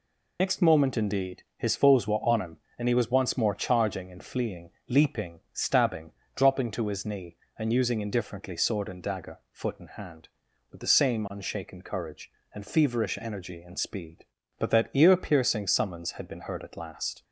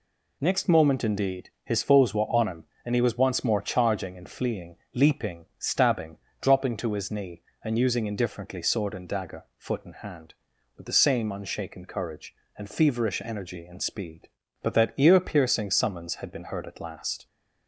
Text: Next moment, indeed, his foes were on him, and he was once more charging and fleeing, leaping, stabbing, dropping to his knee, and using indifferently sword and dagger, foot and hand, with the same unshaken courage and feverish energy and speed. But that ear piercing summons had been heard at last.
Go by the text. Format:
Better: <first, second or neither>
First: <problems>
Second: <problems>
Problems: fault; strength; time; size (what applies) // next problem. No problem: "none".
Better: second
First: loses the start of "Next"; at 0.3 s; 65 ms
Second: none